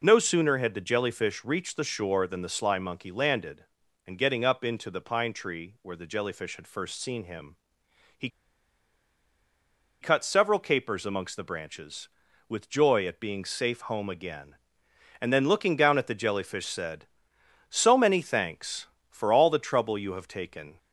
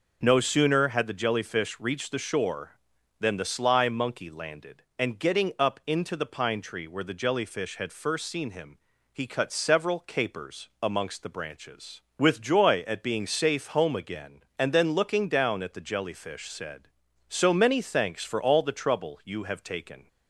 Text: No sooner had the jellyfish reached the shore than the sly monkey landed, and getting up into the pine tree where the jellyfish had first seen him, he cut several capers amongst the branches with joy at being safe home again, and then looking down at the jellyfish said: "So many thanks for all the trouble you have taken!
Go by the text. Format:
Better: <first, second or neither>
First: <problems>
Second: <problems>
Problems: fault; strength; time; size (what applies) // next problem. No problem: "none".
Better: second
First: pauses between "he" and "cut"; strong; at 8.2 s; 1.7 s long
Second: none